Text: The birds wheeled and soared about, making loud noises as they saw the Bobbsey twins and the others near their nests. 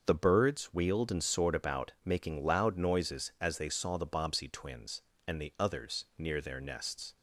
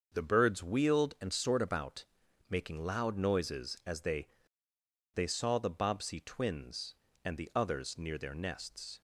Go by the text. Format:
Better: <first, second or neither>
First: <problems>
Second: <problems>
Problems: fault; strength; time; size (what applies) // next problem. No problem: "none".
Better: first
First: starts louder than the rest; until 1.0 s; 6.5 dB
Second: starts louder than the rest; until 1.1 s; 6.5 dB // says "they" twice; at 5.1 s